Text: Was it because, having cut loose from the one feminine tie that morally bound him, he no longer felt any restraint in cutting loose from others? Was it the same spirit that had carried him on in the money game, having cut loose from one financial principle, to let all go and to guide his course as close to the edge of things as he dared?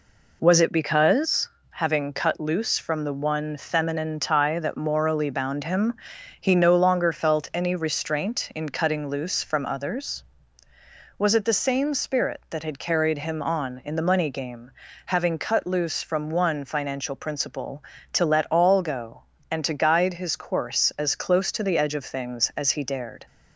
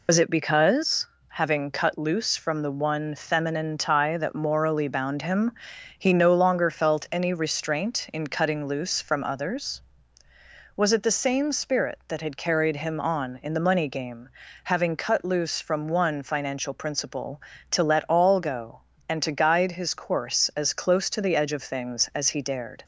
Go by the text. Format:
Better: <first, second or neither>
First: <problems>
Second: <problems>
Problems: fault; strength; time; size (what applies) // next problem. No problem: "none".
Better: first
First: none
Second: loses the start of "Was"; at 0.0 s; 95 ms